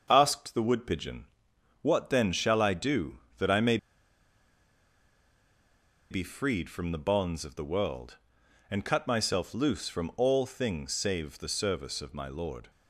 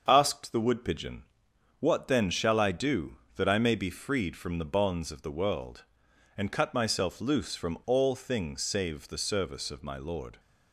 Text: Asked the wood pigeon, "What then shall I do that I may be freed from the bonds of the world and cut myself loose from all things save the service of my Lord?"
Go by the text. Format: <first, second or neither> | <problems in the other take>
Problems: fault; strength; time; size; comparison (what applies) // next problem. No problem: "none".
second | starts louder than the rest; until 1.1 s; 6.5 dB; also in the second // pauses between "may" and "be"; strong; at 3.7 s; 2.3 s long